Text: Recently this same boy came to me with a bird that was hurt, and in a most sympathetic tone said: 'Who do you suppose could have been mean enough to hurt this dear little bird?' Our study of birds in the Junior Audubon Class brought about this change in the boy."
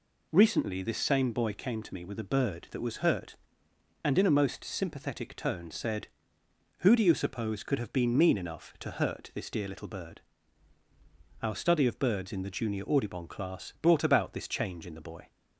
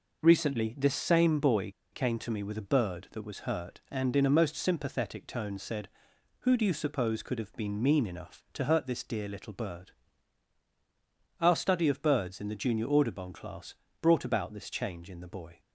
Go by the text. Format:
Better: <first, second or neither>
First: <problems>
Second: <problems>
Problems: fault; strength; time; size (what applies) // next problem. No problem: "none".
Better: first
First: none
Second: pauses between "boy" and "came"; slight; at 1.7 s; 0.21 s long // pauses between "Class" and "brought"; slight; at 13.7 s; 0.28 s long